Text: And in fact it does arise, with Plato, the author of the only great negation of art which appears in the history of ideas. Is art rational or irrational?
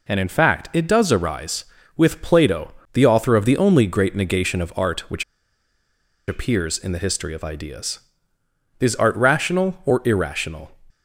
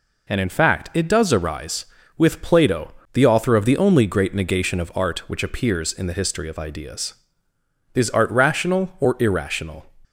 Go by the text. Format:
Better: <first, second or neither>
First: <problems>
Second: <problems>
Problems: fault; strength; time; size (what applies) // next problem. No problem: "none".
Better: second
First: pauses between "which" and "appears"; at 5.2 s; 1.0 s long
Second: none